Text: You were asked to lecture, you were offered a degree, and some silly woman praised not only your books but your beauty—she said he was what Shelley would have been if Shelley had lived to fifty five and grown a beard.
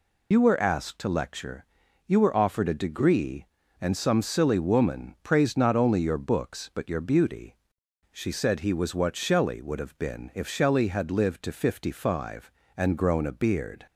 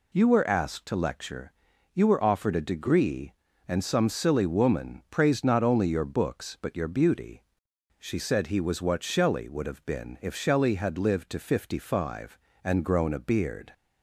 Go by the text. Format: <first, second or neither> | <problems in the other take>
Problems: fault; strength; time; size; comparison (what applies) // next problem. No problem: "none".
second | loses the start of "You"; at 0.3 s; 40 ms